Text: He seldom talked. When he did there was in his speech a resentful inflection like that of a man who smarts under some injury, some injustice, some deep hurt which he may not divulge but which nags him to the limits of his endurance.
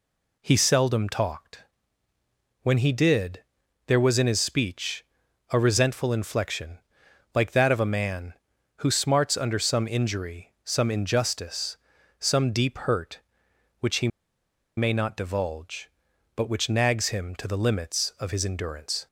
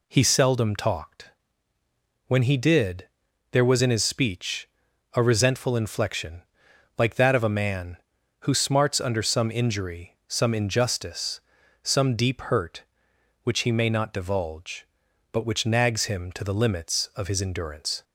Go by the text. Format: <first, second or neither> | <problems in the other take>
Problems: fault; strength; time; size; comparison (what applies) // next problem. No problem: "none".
second | pauses between "did" and "there"; noticeable; at 3.4 s; 0.46 s long; noticeable in the second // pauses between "speech" and "a"; noticeable; at 5.0 s; 0.46 s long; noticeable in the second // pauses between "inflection" and "like"; noticeable; at 6.7 s; 0.56 s long; noticeable in the second // pauses between "he" and "may"; noticeable; at 14.0 s; 0.69 s long